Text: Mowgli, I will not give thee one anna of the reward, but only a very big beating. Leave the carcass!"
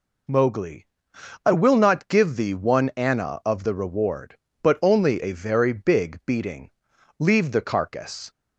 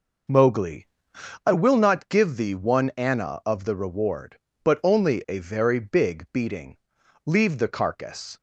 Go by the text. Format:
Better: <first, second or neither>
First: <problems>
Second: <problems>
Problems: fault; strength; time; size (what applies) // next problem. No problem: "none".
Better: first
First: none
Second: starts louder than the rest; noticeable; until 1.5 s; 5.5 dB